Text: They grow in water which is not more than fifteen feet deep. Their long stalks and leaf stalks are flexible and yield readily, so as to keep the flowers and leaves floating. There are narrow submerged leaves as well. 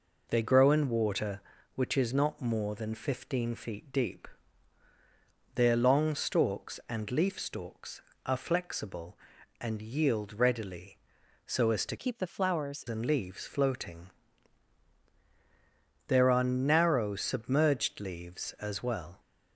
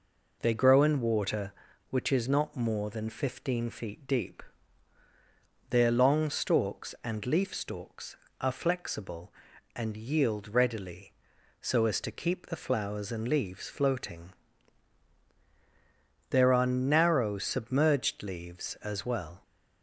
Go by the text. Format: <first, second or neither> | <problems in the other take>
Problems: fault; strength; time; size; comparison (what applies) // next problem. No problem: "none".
second | changes voice from "keep" to "flowers"; from 11.9 to 12.8 s; 0.9 s long